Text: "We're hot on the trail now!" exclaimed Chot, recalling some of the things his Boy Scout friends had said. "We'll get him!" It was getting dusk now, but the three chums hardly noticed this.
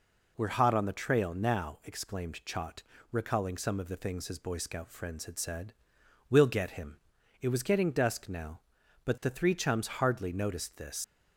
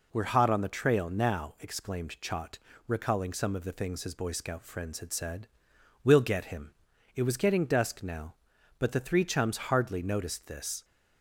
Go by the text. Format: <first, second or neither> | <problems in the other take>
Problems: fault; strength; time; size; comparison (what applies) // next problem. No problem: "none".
second | leaves "this" unfinished; at 11.0 s; 100 ms